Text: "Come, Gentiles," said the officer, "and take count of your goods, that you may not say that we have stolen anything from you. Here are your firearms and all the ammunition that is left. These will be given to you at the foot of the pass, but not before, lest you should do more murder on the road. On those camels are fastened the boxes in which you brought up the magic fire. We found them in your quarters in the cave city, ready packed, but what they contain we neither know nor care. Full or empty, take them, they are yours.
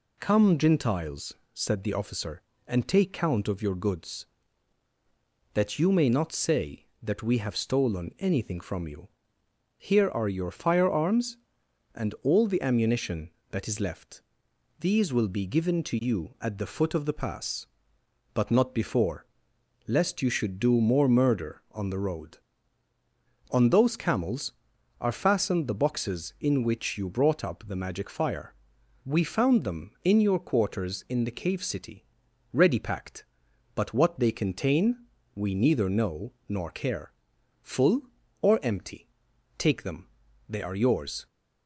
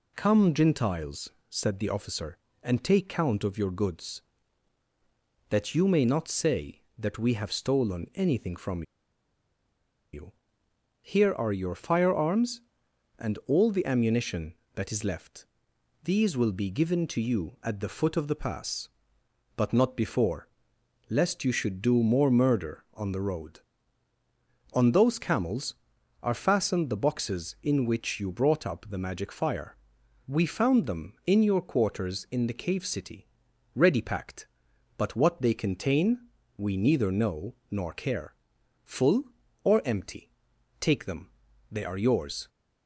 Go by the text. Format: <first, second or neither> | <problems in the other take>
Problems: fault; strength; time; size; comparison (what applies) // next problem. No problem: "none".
first | pauses between "from" and "you"; strong; at 8.8 s; 1.3 s long // pauses between "contain" and "we"; slight; at 36.2 s; 0.28 s long; slight in the first // pauses between "know" and "nor"; slight; at 37.5 s; 0.16 s long; slight in the first